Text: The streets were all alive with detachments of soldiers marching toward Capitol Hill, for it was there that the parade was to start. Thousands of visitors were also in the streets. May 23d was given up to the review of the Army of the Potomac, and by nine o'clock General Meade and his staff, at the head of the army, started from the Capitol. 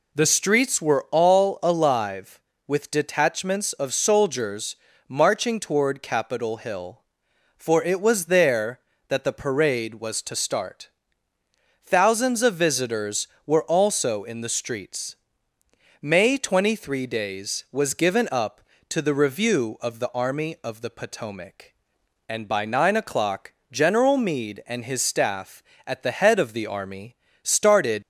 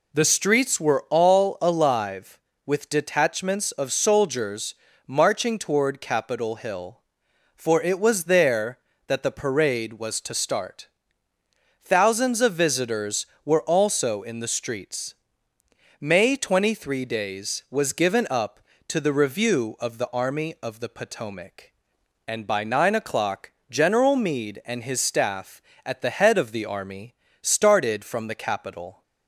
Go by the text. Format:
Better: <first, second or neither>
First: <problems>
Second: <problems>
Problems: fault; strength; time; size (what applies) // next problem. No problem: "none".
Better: second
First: pauses between "soldiers" and "marching"; slight; at 4.7 s; 0.32 s long // pauses between "o'clock" and "General"; slight; at 23.5 s; 0.18 s long // stops before "from the Capitol"; at 28.0 s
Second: pauses between "soldiers" and "marching"; slight; at 4.7 s; 0.32 s long // pauses between "o'clock" and "General"; slight; at 23.5 s; 0.18 s long